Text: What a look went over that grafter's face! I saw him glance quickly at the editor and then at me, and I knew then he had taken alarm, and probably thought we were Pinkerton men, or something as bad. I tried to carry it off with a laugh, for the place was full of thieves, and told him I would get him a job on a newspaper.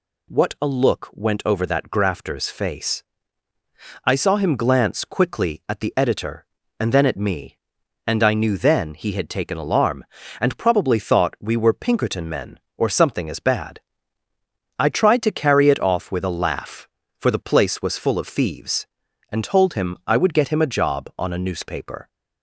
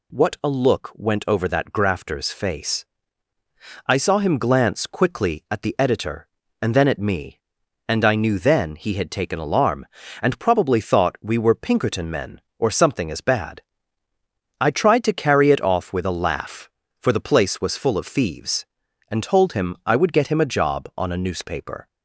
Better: neither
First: none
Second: none

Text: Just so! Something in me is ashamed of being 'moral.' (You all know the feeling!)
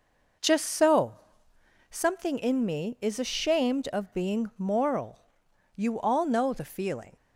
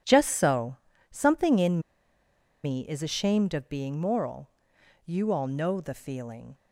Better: first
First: none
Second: pauses between "in" and "me"; noticeable; at 1.8 s; 0.83 s long

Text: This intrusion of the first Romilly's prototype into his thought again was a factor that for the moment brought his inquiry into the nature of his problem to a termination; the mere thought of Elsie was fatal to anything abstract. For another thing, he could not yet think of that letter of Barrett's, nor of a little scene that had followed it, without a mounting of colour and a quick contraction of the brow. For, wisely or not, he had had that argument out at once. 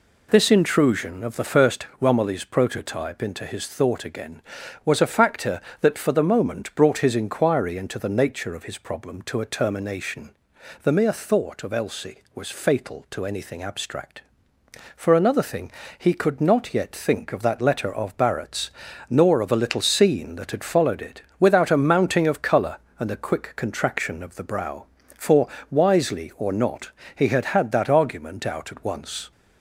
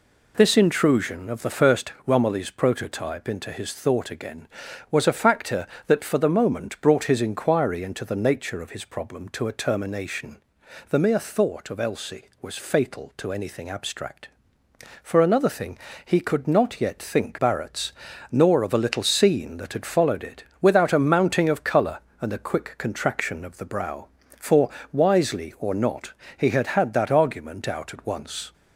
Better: first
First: none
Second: skips "of that letter of"; at 17.3 s

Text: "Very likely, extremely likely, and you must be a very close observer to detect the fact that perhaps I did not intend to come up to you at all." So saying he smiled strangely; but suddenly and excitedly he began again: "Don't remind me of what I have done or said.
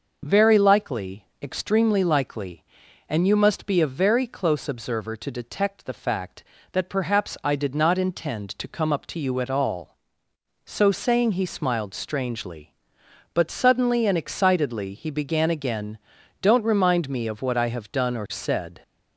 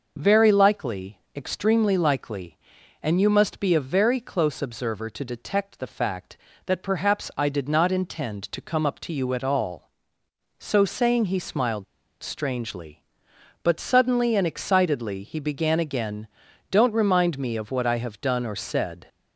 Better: first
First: none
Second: pauses between "smiled" and "strangely"; at 11.8 s; 0.38 s long

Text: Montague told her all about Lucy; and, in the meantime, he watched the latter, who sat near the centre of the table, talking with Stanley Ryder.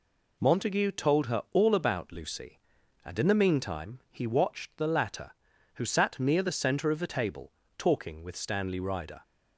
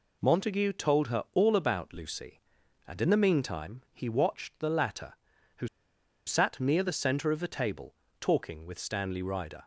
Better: first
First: none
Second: pauses between "who" and "sat"; noticeable; at 5.6 s; 0.58 s long

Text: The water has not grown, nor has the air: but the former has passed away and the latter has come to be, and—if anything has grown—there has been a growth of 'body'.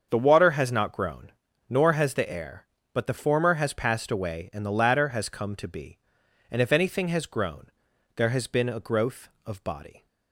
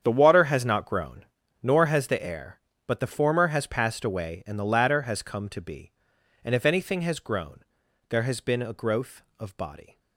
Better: first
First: starts louder than the rest; until 1.1 s; 7 dB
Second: gets quieter; strong; throughout; 15 dB // starts louder than the rest; strong; until 1.0 s; 8 dB

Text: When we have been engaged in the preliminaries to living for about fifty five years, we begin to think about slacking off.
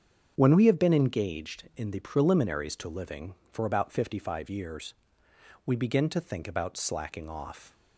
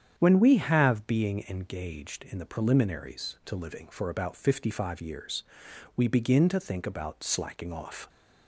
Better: first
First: starts louder than the rest; strong; until 1.3 s; 7.5 dB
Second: starts louder than the rest; strong; until 1.1 s; 8.5 dB // says "being" for "been"; at 1.0 s

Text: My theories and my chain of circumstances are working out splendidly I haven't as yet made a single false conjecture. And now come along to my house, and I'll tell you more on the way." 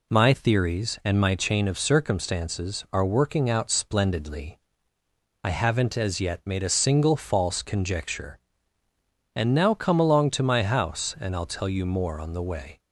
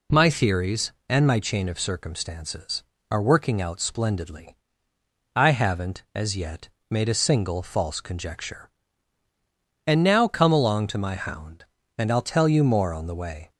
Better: first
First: pauses between "splendidly" and "I"; noticeable; at 4.5 s; 0.84 s long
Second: pauses between "splendidly" and "I"; noticeable; at 4.5 s; 0.80 s long // pauses between "yet" and "made"; slight; at 6.6 s; 0.22 s long // says "hound" for "house"; at 11.1 s

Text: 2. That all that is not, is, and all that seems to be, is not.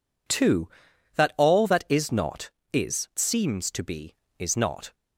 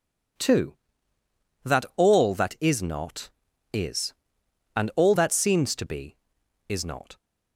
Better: second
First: skips "and all that"; at 3.1 s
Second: none

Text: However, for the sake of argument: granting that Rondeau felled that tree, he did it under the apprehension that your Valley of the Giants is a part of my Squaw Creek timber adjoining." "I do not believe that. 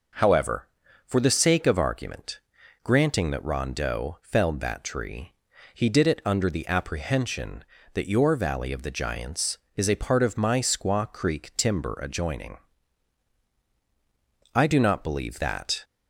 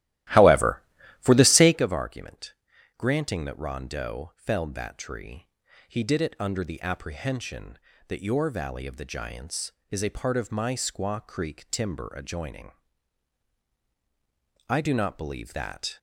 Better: first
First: none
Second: starts louder than the rest; strong; until 1.8 s; 15.5 dB

